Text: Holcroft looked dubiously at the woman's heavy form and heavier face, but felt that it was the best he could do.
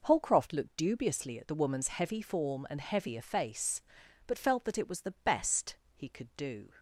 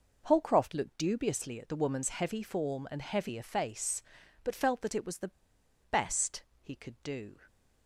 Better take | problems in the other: first | pauses between "the" and "best"; noticeable; at 5.3 s; 0.61 s long // pauses between "best" and "he"; slight; at 6.4 s; 0.20 s long; slight in the first

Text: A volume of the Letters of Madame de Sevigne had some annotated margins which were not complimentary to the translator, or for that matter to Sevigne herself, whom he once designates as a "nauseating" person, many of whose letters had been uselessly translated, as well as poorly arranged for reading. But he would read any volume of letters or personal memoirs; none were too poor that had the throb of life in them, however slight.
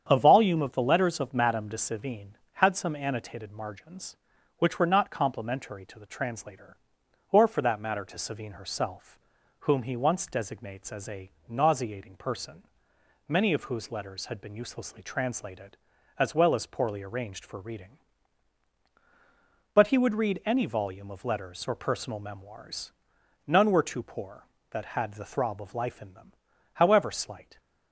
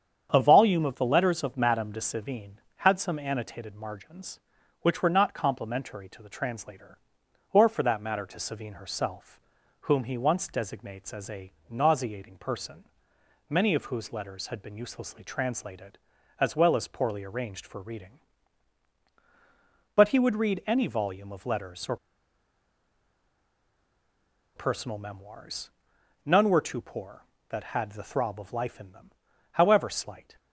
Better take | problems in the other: first | starts louder than the rest; strong; until 1.3 s; 8 dB; strong in the first // pauses between "a" and "nauseating"; slight; at 11.5 s; 0.18 s long; slight in the first // pauses between "or" and "personal"; strong; at 21.9 s; 2.5 s long

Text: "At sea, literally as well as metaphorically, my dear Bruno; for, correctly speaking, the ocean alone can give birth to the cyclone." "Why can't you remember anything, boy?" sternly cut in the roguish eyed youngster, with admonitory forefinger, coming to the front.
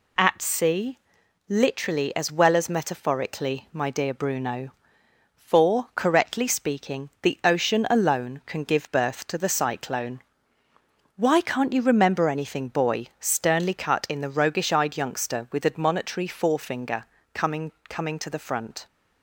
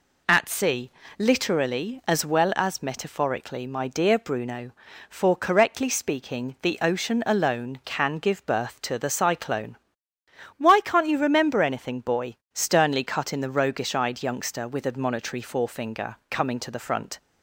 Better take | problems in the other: second | says "coming" twice; at 17.9 s

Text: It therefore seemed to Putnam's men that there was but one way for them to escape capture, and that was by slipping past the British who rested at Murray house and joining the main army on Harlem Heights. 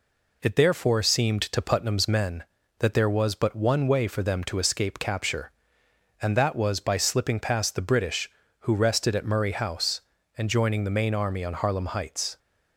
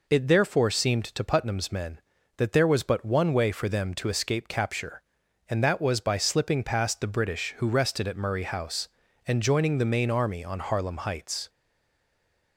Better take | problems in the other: first | stays silent after the last word; from 11.4 s on; 1.1 s long

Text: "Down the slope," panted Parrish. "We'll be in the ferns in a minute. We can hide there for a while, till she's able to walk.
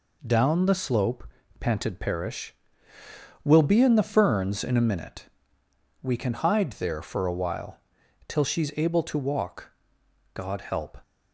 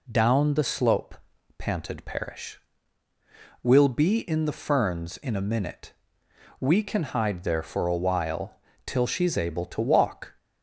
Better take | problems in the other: second | goes on to say "God help"; noticeable; from 10.3 s on; 0.64 s long

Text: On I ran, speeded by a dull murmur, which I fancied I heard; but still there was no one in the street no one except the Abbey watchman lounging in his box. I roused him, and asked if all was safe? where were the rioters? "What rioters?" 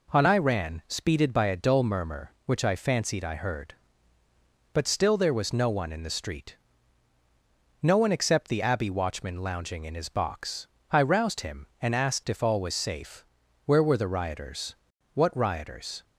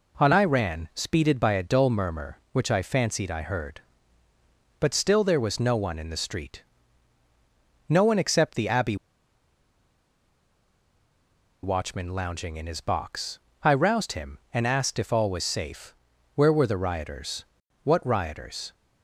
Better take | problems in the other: first | pauses between "street" and "no"; strong; at 6.6 s; 1.2 s long; strong in the first // pauses between "Abbey" and "watchman"; strong; at 8.9 s; 2.6 s long

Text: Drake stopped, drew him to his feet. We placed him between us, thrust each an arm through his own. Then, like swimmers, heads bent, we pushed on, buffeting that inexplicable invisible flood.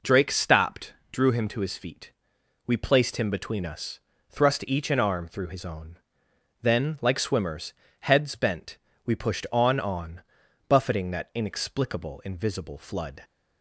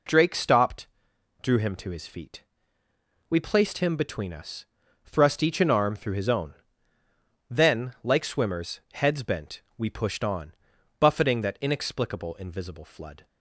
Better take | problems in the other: second | says "on" twice; at 9.7 s

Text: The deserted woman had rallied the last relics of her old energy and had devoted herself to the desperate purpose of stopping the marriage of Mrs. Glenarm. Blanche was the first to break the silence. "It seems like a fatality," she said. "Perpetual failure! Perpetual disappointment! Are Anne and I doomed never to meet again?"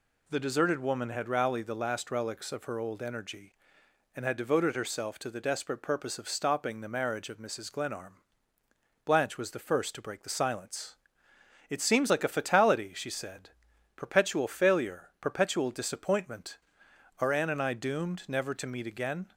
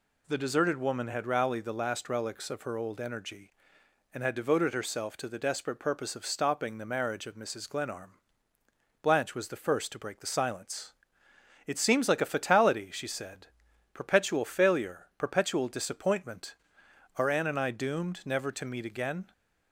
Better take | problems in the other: neither | none

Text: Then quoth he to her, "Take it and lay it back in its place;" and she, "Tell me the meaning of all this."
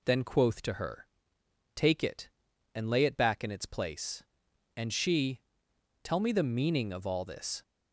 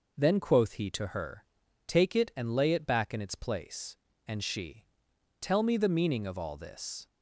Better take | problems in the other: second | skips "he"; at 0.6 s

